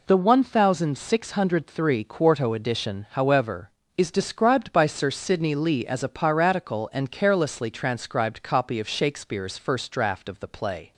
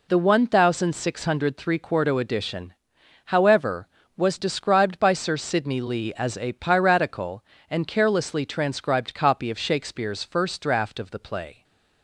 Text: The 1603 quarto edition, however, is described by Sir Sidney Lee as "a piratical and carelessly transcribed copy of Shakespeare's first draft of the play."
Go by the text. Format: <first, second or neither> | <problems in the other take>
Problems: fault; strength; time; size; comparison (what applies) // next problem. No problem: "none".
first | says "was" for "is"; at 4.1 s